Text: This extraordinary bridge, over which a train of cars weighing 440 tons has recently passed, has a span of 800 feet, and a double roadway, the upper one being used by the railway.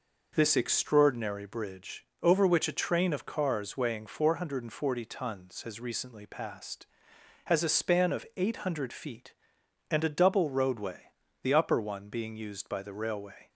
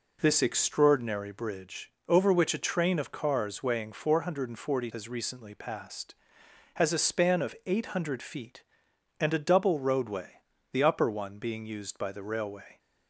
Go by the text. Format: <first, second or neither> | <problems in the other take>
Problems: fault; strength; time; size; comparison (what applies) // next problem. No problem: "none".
first | skips "tons"; at 4.9 s